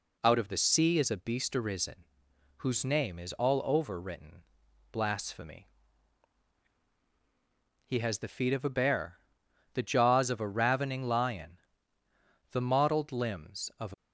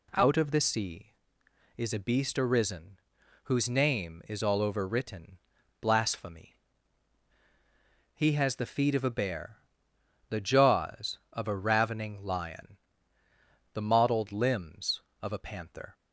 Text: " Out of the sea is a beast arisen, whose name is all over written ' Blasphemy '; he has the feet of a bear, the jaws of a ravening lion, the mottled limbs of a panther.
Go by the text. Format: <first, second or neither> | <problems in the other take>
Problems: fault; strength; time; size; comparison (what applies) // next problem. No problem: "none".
second | stops before "panther"; at 13.9 s